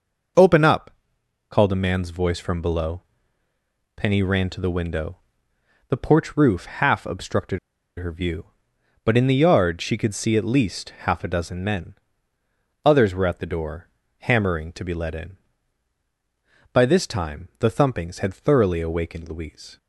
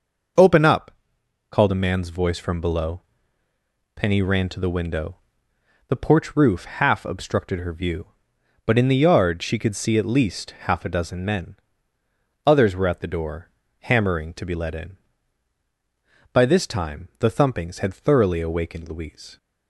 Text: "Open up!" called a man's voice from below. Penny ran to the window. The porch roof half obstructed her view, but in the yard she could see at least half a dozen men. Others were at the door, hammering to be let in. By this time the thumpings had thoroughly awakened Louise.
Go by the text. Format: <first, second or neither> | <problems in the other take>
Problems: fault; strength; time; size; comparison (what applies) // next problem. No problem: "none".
second | pauses between "obstructed" and "her"; at 7.5 s; 0.40 s long // pauses between "least" and "half"; slight; at 10.8 s; 0.16 s long; slight in the second